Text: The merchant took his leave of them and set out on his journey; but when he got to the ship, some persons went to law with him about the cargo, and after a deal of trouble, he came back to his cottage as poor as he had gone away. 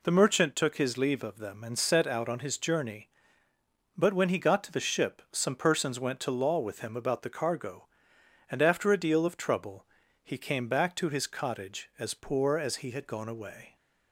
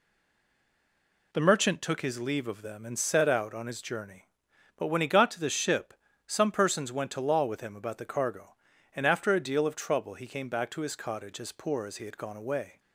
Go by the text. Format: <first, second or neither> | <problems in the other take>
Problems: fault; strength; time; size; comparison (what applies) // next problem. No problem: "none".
first | stays silent before the first word; noticeable; until 1.3 s; 1.3 s long